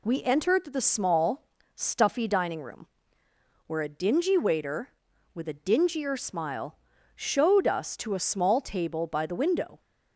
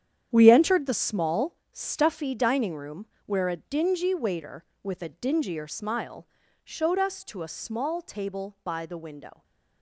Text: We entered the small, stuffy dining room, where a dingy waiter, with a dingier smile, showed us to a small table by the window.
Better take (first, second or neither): first